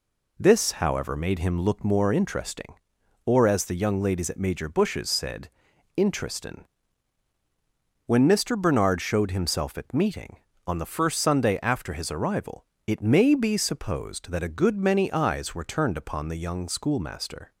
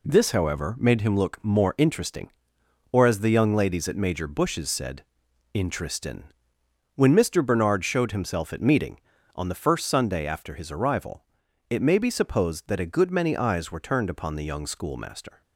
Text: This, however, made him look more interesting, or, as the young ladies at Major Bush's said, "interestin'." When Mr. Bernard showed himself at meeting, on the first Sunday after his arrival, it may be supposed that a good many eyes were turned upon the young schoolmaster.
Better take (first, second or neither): neither